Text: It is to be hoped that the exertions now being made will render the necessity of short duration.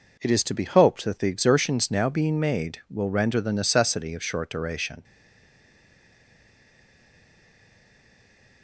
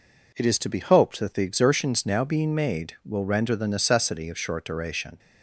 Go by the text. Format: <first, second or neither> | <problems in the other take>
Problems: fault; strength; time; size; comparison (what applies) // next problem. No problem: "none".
second | stays silent after the last word; strong; from 5.0 s on; 3.6 s long